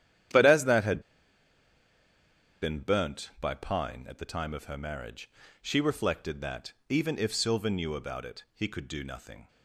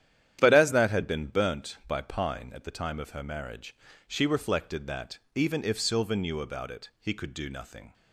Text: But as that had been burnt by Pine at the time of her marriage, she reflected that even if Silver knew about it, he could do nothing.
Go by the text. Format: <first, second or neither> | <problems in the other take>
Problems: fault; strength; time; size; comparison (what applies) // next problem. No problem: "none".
second | starts louder than the rest; strong; until 2.9 s; 10.5 dB; strong in the second // pauses between "had" and "been"; strong; at 1.0 s; 1.6 s long // pauses between "that" and "even"; slight; at 6.7 s; 0.16 s long; slight in the second